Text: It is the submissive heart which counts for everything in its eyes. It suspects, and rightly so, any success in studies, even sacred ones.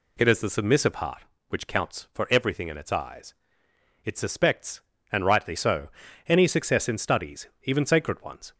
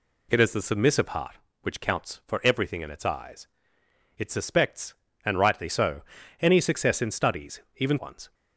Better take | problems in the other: first | skips "sacred"; at 7.9 s

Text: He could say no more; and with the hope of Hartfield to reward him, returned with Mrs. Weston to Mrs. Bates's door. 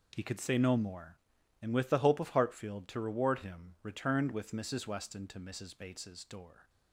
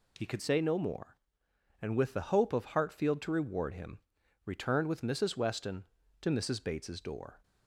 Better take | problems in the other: first | changes voice at "say"; from 0.4 s on; 7.0 s long

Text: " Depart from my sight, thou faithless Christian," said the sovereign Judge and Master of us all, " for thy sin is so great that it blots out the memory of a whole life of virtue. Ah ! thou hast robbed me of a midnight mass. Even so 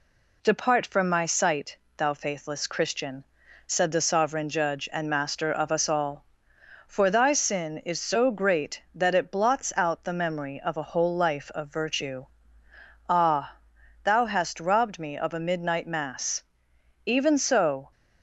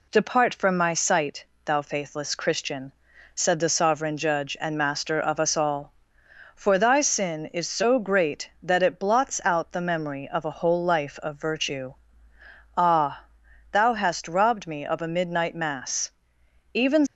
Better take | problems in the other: first | stops before "so"; at 17.0 s

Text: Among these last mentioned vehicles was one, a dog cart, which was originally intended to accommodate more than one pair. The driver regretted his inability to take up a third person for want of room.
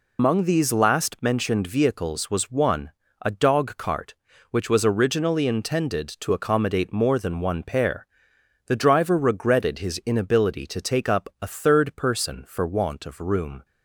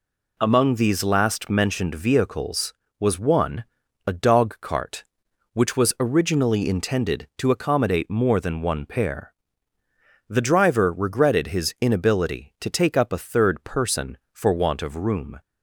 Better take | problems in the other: second | loses the start of "Among"; at 0.1 s; 125 ms

